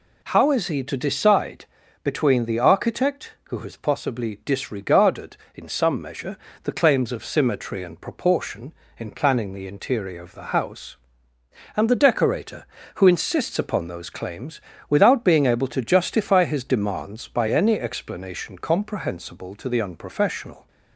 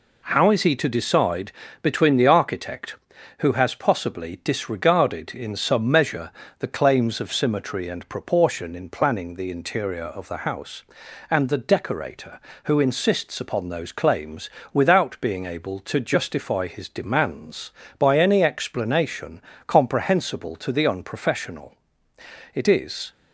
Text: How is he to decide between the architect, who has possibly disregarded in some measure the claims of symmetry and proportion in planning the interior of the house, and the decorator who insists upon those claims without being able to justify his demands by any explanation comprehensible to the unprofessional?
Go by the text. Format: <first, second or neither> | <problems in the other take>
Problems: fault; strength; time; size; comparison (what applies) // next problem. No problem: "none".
first | pauses between "decide" and "between"; slight; at 1.5 s; 0.32 s long; also in the first // pauses between "measure" and "the"; slight; at 6.3 s; 0.28 s long; slight in the first // pauses between "claims" and "without"; slight; at 14.4 s; 0.24 s long; slight in the first // pauses between "explanation" and "comprehensible"; slight; at 19.4 s; 0.24 s long // goes on to say "It is"; from 22.5 s on; 0.58 s long